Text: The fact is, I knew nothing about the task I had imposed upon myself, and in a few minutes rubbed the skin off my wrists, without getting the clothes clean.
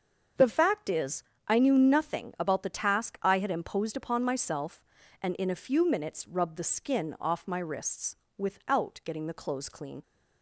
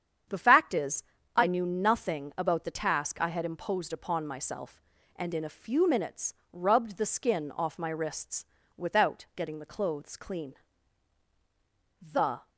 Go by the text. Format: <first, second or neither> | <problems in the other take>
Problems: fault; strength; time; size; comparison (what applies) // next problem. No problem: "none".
first | starts louder than the rest; strong; until 1.6 s; 8.5 dB; also in the first // pauses between "minutes" and "rubbed"; slight; at 6.3 s; 0.20 s long // goes on to say "The"; slight; from 12.0 s on; 0.48 s long